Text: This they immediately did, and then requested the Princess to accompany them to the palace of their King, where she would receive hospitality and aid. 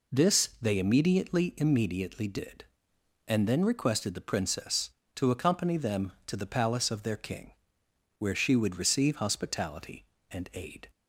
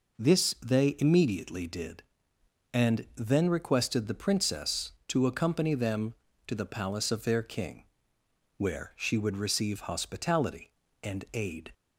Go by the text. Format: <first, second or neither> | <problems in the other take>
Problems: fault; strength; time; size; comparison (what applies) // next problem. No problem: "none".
second | says "immediately" twice; at 1.5 s